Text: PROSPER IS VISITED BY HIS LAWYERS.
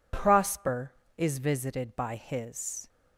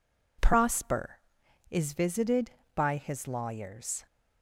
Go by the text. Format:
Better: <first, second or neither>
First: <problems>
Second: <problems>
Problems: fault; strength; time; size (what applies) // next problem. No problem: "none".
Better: second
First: stops before "LAWYERS"; at 2.8 s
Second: none